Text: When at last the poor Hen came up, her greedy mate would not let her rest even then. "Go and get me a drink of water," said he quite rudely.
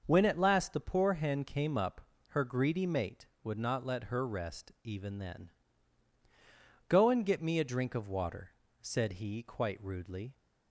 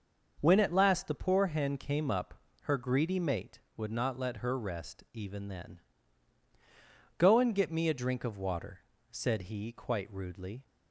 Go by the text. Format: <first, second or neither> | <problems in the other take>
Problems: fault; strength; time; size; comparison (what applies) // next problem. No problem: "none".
neither | starts louder than the rest; the same in both